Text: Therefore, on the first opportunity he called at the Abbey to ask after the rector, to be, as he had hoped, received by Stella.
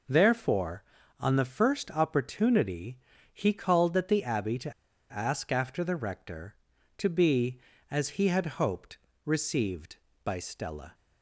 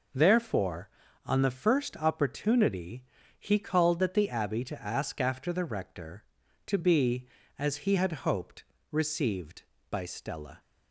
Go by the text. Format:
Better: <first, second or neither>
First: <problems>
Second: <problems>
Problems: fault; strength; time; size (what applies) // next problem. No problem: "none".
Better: second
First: pauses between "opportunity" and "he"; slight; at 2.9 s; 0.34 s long // pauses between "to" and "ask"; at 4.7 s; 0.38 s long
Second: pauses between "opportunity" and "he"; slight; at 3.0 s; 0.34 s long